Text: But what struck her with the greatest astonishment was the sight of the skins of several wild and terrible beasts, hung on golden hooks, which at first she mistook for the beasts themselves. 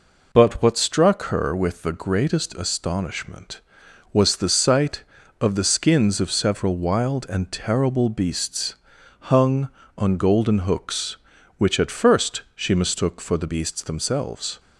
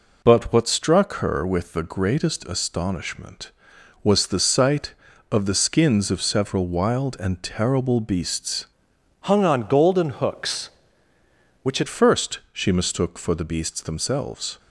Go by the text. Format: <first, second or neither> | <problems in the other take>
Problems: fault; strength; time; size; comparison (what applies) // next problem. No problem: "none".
first | changes voice from "hung" to "at"; from 9.2 to 11.8 s; 2.6 s long